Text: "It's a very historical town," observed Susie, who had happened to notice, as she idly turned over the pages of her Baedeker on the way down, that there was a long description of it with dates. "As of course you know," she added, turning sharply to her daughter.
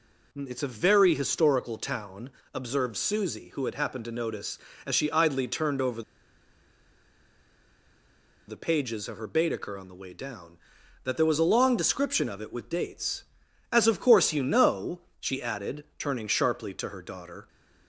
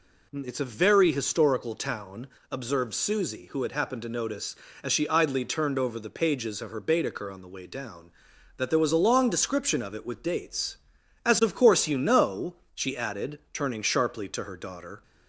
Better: second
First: pauses between "over" and "the"; strong; at 6.0 s; 2.4 s long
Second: none

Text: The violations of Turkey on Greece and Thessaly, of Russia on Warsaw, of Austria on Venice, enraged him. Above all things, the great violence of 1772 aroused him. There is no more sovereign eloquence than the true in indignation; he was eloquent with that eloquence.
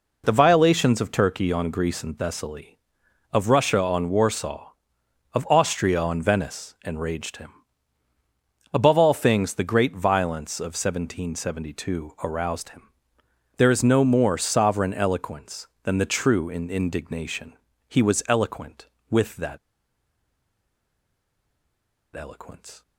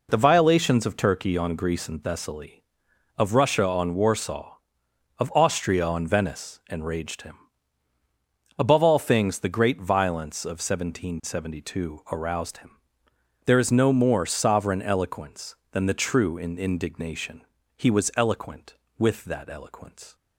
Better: second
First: pauses between "that" and "eloquence"; strong; at 19.5 s; 2.5 s long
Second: none

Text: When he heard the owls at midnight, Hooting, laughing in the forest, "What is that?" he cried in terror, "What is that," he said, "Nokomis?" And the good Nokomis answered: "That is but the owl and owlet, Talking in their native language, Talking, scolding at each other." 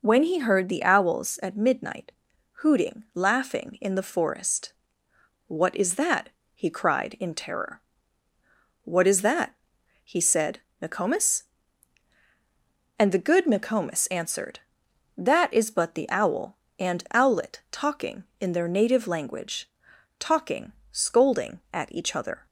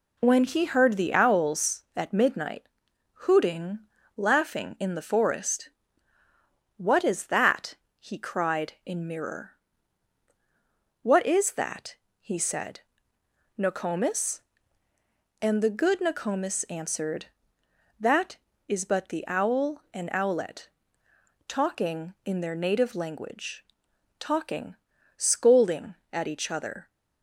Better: first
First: none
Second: says "mirror" for "terror"; at 9.0 s

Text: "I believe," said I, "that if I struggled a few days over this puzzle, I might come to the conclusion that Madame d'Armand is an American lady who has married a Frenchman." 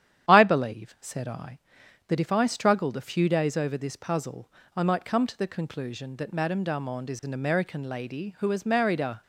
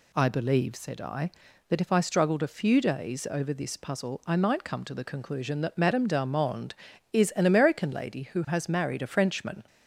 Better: second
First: starts louder than the rest; strong; until 1.3 s; 10 dB // stops before "Frenchman"; at 9.2 s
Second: none

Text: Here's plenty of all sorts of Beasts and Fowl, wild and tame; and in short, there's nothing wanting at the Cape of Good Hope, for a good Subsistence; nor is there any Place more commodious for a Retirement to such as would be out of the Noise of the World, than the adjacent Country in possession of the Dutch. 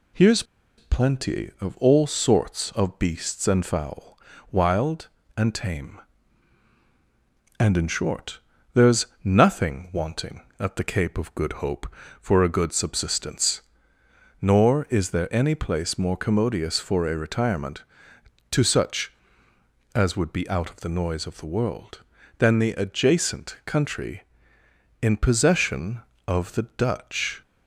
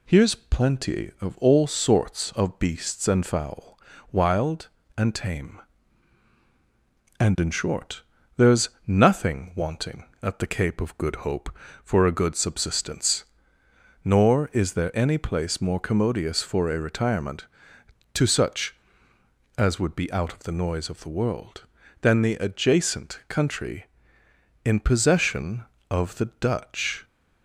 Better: second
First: pauses between "Here's" and "plenty"; slight; at 0.4 s; 0.34 s long // pauses between "there's" and "nothing"; slight; at 9.0 s; 0.16 s long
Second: pauses between "there's" and "nothing"; slight; at 8.7 s; 0.16 s long

